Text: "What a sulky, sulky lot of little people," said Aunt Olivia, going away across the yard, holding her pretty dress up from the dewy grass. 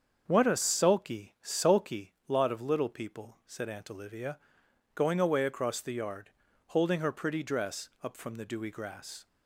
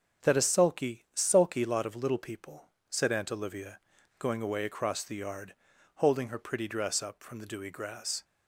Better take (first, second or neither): first